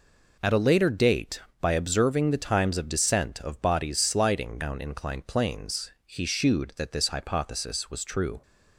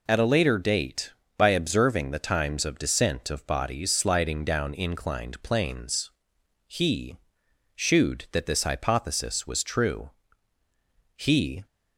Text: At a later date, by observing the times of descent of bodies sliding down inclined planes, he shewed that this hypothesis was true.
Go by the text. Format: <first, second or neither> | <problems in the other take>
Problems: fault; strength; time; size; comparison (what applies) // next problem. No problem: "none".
first | pauses between "he" and "shewed"; noticeable; at 7.1 s; 0.56 s long // goes on to say "He"; from 11.1 s on; 0.50 s long